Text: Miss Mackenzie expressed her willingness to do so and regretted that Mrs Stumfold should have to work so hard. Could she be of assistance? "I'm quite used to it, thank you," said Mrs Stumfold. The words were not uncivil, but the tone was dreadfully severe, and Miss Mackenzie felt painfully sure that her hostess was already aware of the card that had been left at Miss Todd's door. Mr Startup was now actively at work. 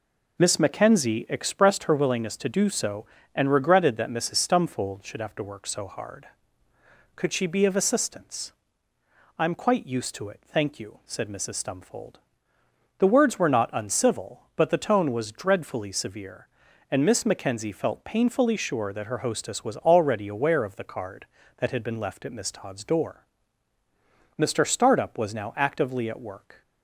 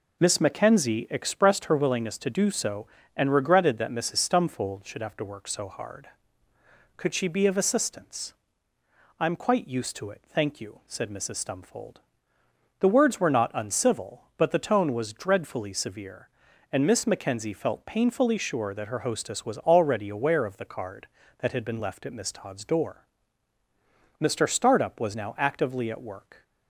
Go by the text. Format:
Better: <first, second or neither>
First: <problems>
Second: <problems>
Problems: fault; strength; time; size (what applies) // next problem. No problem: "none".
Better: neither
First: none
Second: none